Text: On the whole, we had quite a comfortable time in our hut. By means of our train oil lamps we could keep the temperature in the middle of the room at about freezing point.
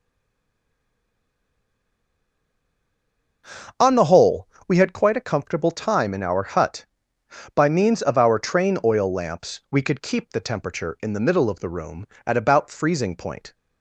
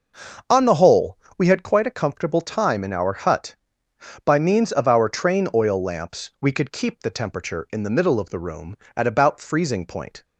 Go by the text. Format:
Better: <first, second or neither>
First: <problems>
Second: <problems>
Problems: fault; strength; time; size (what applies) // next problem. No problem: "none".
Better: second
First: stays silent before the first word; strong; until 3.4 s; 3.4 s long // starts louder than the rest; until 4.9 s; 6 dB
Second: starts louder than the rest; until 1.6 s; 6 dB